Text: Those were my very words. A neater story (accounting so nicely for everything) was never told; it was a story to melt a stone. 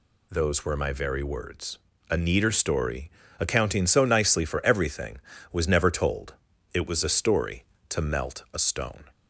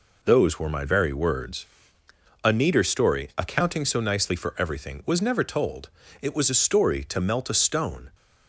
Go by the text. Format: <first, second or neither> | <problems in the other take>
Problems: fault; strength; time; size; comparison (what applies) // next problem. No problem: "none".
neither | none